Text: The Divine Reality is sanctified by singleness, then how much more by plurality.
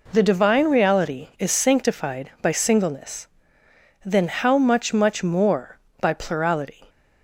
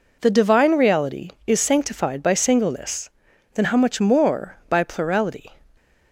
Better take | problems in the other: second | says "much" twice; at 4.9 s

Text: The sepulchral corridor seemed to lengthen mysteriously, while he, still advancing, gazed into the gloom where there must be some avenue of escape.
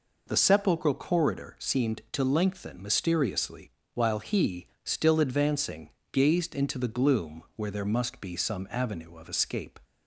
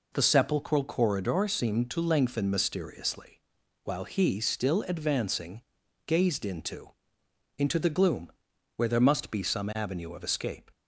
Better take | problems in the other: first | says "into" twice; at 7.5 s // pauses between "gloom" and "where"; noticeable; at 8.3 s; 0.46 s long

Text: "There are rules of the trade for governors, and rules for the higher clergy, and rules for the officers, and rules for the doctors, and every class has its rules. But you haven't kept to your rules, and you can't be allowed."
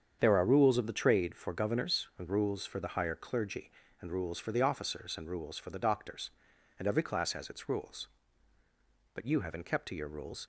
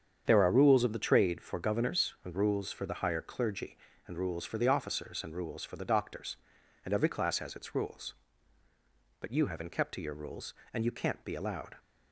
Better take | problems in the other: second | starts louder than the rest; strong; until 1.2 s; 7.5 dB; strong in the second // stops before "and you can't be allowed"; at 10.4 s

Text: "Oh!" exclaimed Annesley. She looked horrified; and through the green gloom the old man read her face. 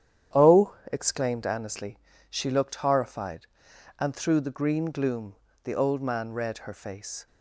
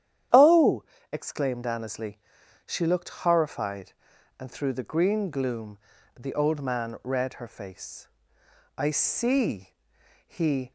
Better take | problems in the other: first | starts louder than the rest; strong; until 1.5 s; 10.5 dB; strong in the first // pauses between "gloom" and "the"; at 5.7 s; 0.40 s long; slight in the first // goes on to say "I see he"; strong; from 8.7 s on; 1.9 s long

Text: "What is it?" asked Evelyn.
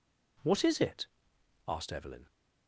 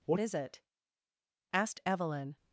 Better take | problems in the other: first | changes voice at "is"; from 0.1 s on; 2.2 s long

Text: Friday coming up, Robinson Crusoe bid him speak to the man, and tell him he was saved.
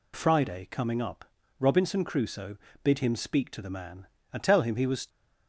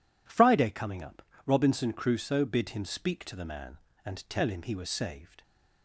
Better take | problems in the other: second | pauses between "Crusoe" and "bid"; slight; at 2.5 s; 0.26 s long // stops before "saved"; at 5.0 s

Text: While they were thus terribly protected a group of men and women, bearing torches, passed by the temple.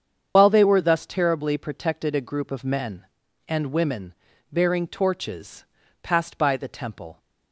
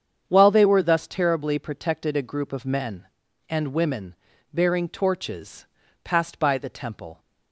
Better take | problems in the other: second | loses the start of "While"; at 0.3 s; 90 ms // starts louder than the rest; strong; until 1.3 s; 7.5 dB; strong in the second

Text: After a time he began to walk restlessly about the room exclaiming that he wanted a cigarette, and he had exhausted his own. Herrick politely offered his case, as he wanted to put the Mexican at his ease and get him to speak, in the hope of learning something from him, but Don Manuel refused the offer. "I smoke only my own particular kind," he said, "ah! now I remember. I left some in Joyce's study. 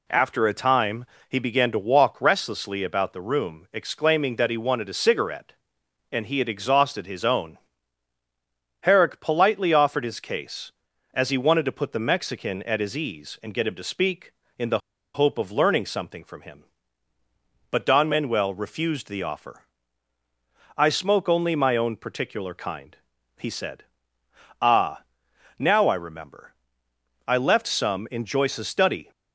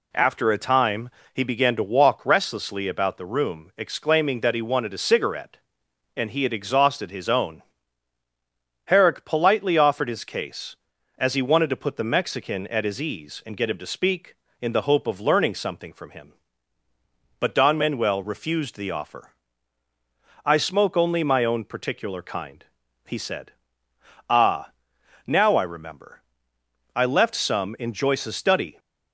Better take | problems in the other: second | pauses between "time" and "he"; slight; at 1.0 s; 0.24 s long; slight in the second // pauses between "the" and "hope"; slight; at 14.7 s; 0.35 s long

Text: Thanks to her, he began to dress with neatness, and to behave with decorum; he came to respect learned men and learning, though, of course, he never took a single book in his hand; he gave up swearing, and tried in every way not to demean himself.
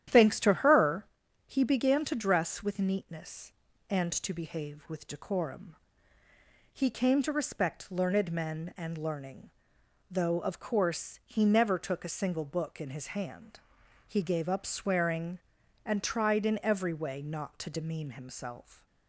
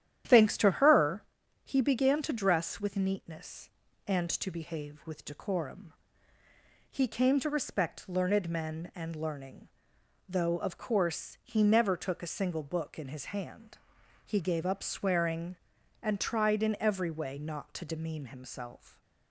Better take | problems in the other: neither | starts louder than the rest; strong; the same in both

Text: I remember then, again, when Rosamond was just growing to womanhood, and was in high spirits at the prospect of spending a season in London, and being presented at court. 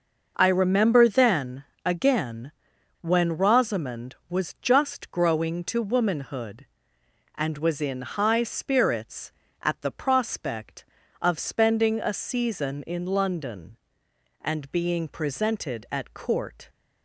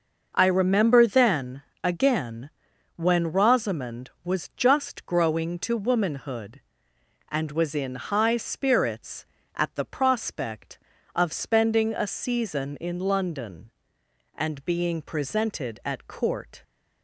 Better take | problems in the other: neither | none

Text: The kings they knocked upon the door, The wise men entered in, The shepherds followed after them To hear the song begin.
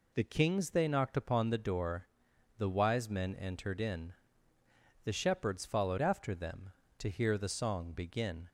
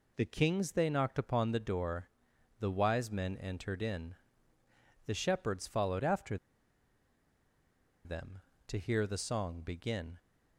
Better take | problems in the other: first | pauses between "after" and "them"; strong; at 6.3 s; 1.6 s long

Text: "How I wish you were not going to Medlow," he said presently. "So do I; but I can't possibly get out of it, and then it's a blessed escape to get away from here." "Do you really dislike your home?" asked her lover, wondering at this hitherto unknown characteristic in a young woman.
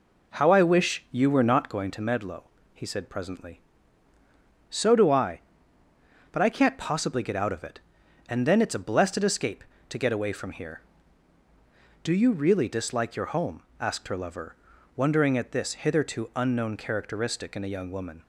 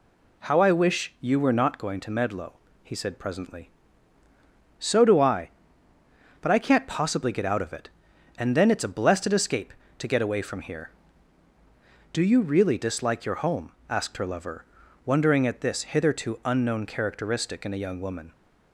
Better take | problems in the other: second | starts louder than the rest; until 2.2 s; 4 dB

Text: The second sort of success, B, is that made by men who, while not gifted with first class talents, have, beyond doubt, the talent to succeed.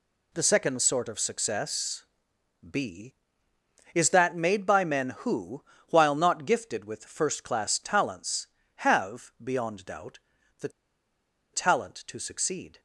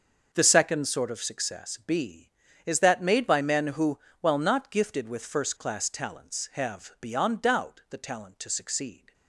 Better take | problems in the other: second | pauses between "the" and "talent"; noticeable; at 10.6 s; 0.83 s long

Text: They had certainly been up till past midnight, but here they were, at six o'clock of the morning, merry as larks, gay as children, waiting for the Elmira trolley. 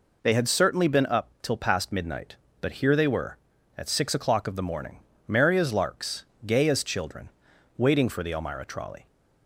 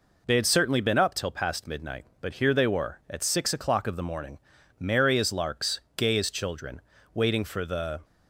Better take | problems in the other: first | stops before "Elmira trolley"; at 8.0 s

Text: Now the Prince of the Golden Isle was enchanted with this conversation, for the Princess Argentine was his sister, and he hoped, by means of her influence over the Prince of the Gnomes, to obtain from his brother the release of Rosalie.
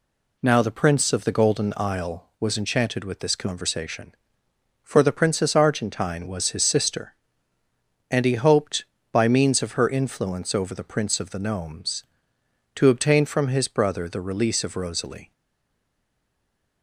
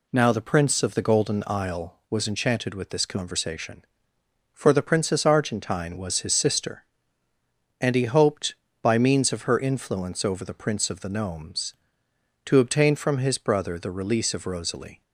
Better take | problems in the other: second | stays silent after the last word; noticeable; from 15.3 s on; 1.5 s long

